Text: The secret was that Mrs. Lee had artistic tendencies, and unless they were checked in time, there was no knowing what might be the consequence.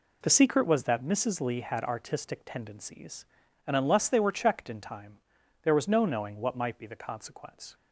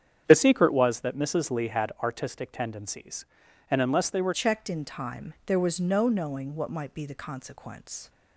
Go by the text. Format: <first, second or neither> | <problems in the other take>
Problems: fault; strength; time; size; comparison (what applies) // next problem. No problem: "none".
first | starts louder than the rest; strong; until 1.2 s; 9 dB // changes voice at "checked"; from 4.3 s on; 3.7 s long